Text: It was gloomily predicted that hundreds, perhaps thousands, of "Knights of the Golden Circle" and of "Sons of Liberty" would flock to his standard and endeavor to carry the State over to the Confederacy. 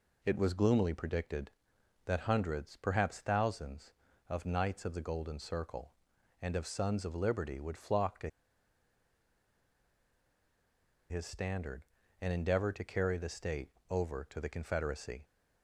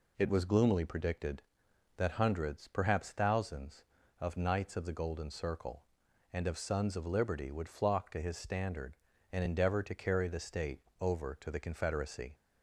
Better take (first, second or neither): second